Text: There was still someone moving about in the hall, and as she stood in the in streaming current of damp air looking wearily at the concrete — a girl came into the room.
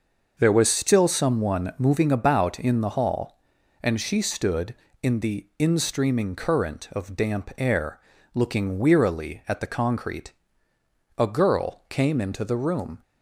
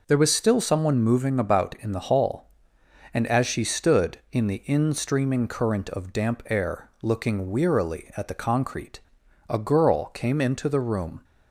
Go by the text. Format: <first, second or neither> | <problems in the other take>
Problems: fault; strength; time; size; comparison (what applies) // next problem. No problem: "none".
second | starts louder than the rest; noticeable; until 1.3 s; 6 dB // skips "as"; at 3.9 s // pauses between "air" and "looking"; slight; at 7.9 s; 0.36 s long